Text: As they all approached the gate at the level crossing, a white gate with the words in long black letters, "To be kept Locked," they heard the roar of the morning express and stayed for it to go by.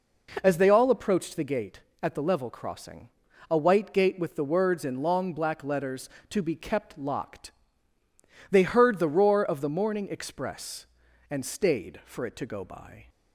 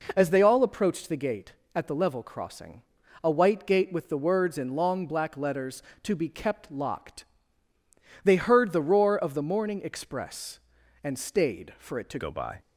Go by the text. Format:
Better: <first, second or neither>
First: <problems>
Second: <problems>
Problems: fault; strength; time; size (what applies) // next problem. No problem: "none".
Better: first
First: none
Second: changes voice at "go"; from 12.1 s on; 0.5 s long